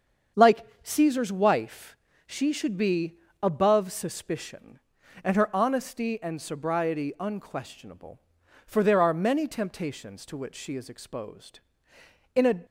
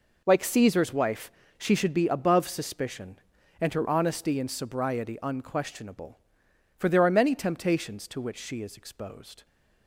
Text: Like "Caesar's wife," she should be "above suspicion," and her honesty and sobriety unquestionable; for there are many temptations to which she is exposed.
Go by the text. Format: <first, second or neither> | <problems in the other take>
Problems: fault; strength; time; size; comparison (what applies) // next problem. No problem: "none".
second | starts louder than the rest; strong; until 1.5 s; 7 dB // pauses between "Like" and "Caesar's"; slight; at 0.6 s; 0.16 s long // pauses between "be" and "above"; slight; at 3.1 s; 0.24 s long // goes on to say "In a"; slight; from 12.3 s on; 0.30 s long